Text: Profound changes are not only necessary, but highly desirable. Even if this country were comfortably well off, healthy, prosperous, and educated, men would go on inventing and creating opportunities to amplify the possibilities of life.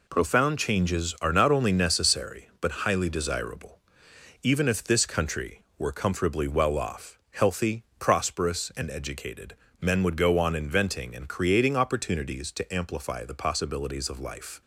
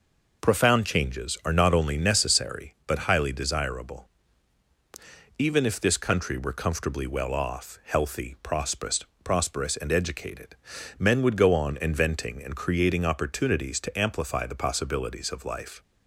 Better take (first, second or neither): first